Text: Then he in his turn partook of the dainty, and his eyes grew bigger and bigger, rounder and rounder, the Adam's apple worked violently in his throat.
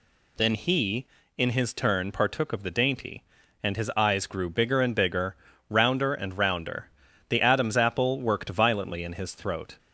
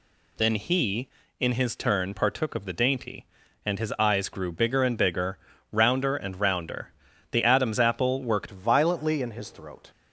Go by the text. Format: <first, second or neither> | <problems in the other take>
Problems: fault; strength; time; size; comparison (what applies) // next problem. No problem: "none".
first | changes voice at "violently"; from 8.5 s on; 1.4 s long